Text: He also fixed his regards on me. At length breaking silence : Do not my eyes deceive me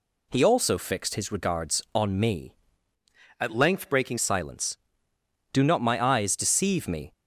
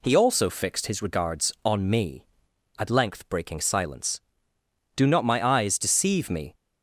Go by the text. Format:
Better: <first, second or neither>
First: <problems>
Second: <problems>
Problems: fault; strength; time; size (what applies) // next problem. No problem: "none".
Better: second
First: changes voice from "At" to "breaking"; from 3.4 to 4.1 s; 0.7 s long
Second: none